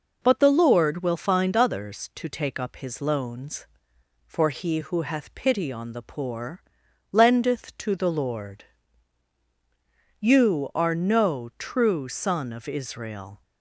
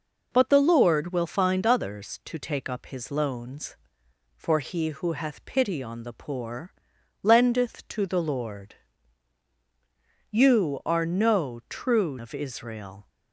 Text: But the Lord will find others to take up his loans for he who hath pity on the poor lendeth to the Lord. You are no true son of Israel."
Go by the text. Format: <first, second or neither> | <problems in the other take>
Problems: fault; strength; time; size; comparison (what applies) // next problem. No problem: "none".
first | pauses between "poor" and "lendeth"; noticeable; at 6.7 s; 0.50 s long; noticeable in the first // skips "son"; at 12.1 s